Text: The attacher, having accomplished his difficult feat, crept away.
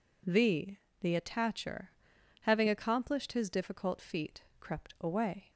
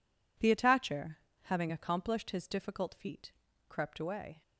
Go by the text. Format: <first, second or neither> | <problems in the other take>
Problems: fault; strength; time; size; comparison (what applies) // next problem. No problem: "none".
second | says "The" twice; at 1.0 s